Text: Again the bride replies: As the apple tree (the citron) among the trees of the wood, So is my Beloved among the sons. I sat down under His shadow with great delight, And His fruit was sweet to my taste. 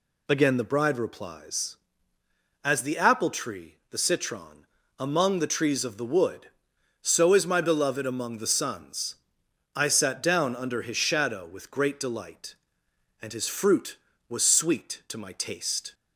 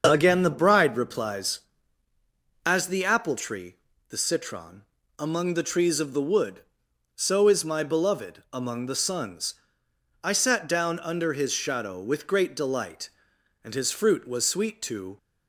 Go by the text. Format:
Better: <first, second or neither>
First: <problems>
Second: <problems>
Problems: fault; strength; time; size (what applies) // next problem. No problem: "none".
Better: first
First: none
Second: starts louder than the rest; until 1.1 s; 6.5 dB // stops before "my taste"; at 15.1 s